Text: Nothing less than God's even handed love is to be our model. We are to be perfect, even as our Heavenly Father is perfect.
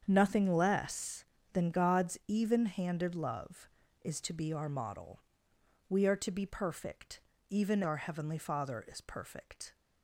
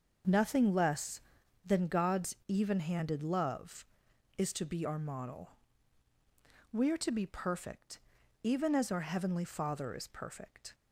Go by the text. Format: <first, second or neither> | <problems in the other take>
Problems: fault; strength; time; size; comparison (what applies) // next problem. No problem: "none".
second | starts louder than the rest; strong; until 1.0 s; 7.5 dB; also in the second // skips "as"; at 7.8 s